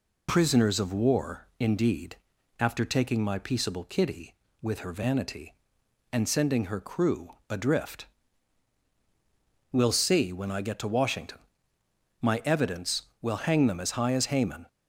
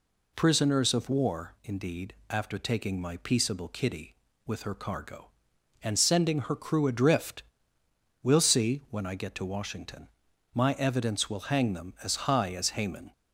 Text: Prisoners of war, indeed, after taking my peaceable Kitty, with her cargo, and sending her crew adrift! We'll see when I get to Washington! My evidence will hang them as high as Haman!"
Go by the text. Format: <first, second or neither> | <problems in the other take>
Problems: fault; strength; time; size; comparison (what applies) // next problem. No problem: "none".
second | says "vanity" for "cargo"; at 4.9 s // pauses between "crew" and "adrift"; slight; at 7.3 s; 0.16 s long